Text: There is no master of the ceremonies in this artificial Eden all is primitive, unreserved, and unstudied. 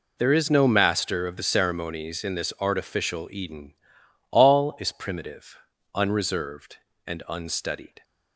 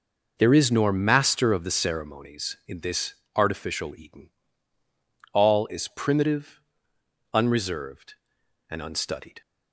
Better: first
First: pauses between "Eden" and "all"; noticeable; at 3.7 s; 0.56 s long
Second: says "nor" for "no"; at 0.7 s // pauses between "this" and "artificial"; slight; at 3.1 s; 0.20 s long // pauses between "Eden" and "all"; at 4.2 s; 1.0 s long

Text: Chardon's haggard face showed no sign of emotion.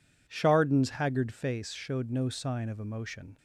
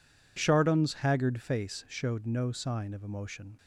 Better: neither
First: none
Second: none

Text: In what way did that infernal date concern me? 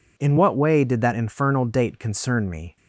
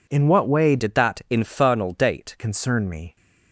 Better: first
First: none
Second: changes voice from "did" to "date"; from 0.7 to 2.3 s; 1.6 s long

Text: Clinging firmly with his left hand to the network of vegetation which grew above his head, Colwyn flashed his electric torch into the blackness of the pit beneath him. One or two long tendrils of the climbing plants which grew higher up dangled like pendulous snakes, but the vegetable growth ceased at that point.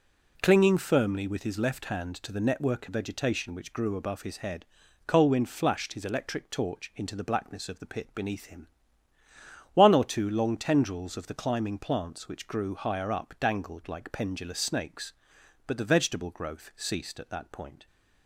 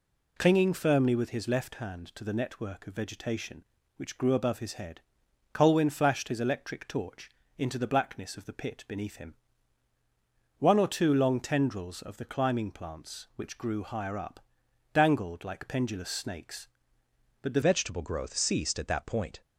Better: first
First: none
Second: pauses between "torch" and "into"; slight; at 7.3 s; 0.26 s long // pauses between "up" and "dangled"; noticeable; at 14.4 s; 0.52 s long // changes voice at "vegetable"; from 17.6 s on; 1.8 s long

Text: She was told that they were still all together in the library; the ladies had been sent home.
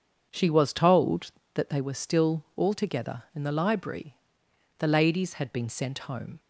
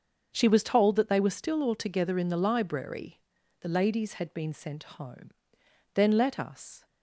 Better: first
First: starts louder than the rest; until 1.3 s; 7 dB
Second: starts louder than the rest; until 1.3 s; 6.5 dB // goes on to say "Then let us"; noticeable; from 5.9 s on; 0.92 s long

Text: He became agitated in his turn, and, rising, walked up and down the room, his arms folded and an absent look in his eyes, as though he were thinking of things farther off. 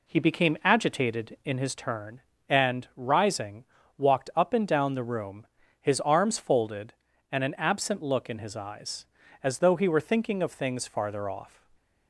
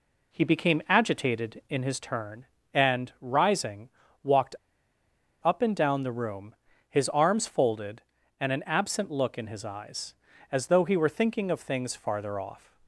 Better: first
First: none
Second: pauses between "walked" and "up"; noticeable; at 4.5 s; 0.88 s long

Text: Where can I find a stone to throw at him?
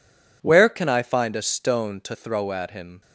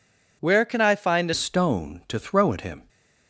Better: first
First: none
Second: changes voice at "stone"; from 1.3 s on; 1.5 s long

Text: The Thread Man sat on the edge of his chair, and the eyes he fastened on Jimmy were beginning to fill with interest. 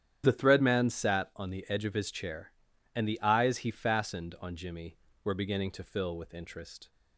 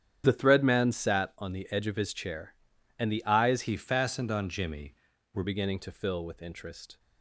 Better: first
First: starts louder than the rest; strong; until 1.2 s; 10 dB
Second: starts louder than the rest; strong; until 1.2 s; 9.5 dB // changes voice from "he" to "were"; from 3.6 to 5.4 s; 1.8 s long

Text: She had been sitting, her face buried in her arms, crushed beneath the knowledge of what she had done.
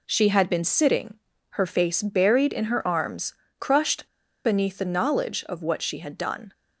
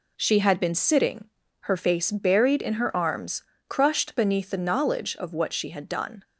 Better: second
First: pauses between "crushed" and "beneath"; at 4.0 s; 0.39 s long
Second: none

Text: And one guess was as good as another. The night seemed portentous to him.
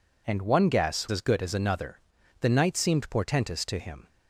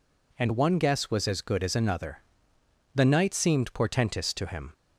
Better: second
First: skips "was"; at 1.0 s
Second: none

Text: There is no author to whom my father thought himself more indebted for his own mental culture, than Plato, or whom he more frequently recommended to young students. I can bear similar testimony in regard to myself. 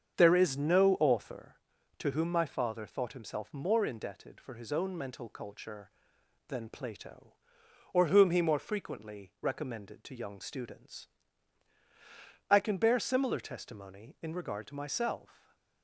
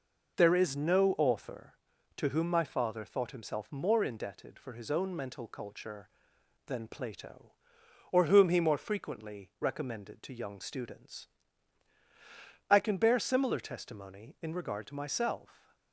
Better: second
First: starts louder than the rest; strong; until 1.4 s; 7.5 dB // stays silent after the last word; slight; from 15.3 s on; 0.5 s long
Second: none

